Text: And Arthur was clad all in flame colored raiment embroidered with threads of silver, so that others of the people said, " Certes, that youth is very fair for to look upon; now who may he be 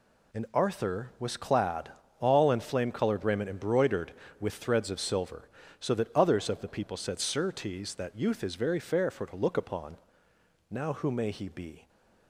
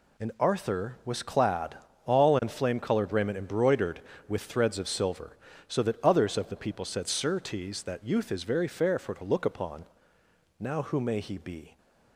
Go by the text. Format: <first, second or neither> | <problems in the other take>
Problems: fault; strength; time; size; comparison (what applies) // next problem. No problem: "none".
neither | pauses between "clad" and "all"; slight; the same in both